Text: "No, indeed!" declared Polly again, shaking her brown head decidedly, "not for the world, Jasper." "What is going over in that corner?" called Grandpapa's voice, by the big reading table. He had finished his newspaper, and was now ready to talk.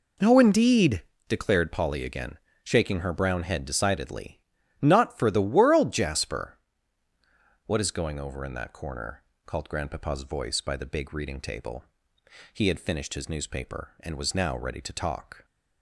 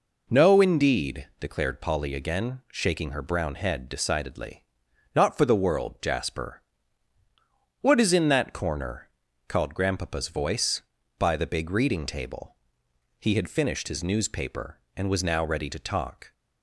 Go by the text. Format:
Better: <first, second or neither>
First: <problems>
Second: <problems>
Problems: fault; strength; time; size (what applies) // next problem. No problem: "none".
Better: first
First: none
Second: skips "going over"; at 8.1 s